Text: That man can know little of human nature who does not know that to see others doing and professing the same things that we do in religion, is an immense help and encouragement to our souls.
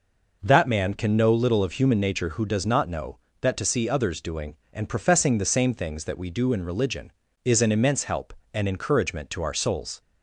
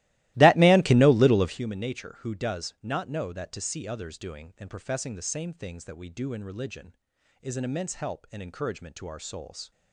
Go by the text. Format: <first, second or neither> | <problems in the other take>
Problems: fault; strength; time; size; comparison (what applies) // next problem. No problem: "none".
first | starts louder than the rest; strong; until 1.6 s; 17.5 dB